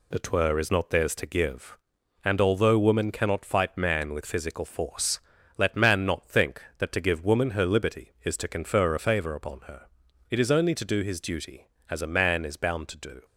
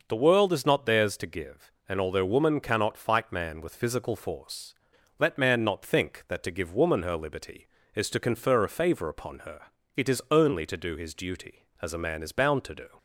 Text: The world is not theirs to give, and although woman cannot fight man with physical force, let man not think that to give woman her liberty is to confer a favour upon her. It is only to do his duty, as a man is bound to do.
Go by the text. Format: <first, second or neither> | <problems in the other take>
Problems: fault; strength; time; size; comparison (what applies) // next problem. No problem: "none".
second | says "twer" for "world"; at 0.1 s